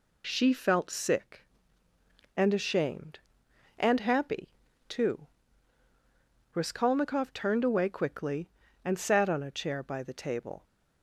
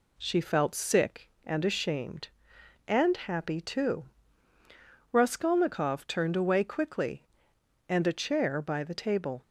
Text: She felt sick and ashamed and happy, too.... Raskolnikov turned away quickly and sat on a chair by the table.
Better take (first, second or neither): first